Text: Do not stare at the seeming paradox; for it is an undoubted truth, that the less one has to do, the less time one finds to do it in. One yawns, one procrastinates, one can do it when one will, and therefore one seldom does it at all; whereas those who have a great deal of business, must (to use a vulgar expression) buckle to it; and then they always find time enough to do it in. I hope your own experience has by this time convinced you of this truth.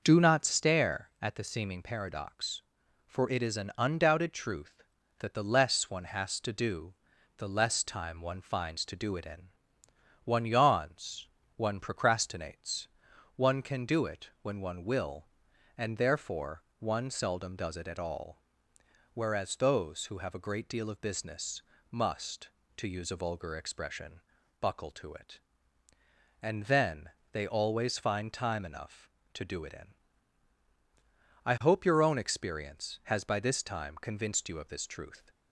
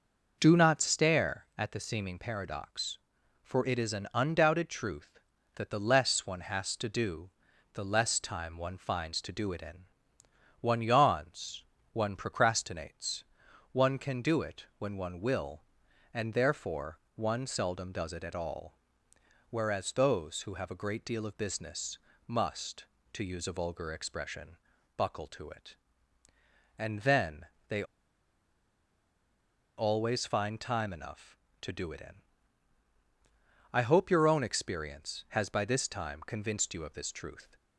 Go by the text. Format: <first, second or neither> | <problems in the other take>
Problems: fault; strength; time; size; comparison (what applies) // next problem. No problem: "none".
first | pauses between "therefore" and "one"; slight; at 16.9 s; 0.16 s long; slight in the first // pauses between "then" and "they"; slight; at 27.4 s; 0.24 s long; slight in the first // pauses between "they" and "always"; strong; at 27.8 s; 1.9 s long